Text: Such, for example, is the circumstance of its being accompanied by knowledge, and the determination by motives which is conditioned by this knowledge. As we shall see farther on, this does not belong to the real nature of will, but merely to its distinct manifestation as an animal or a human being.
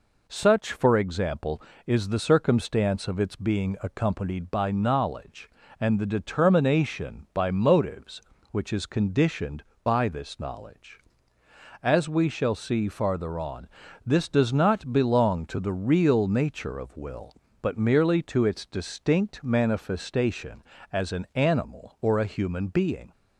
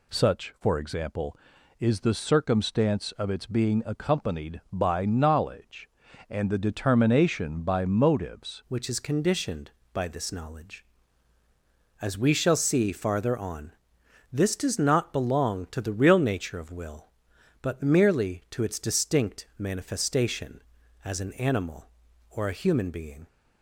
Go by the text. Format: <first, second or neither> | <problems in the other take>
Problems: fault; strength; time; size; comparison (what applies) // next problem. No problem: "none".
first | changes voice at "which"; from 8.6 s on; 14.6 s long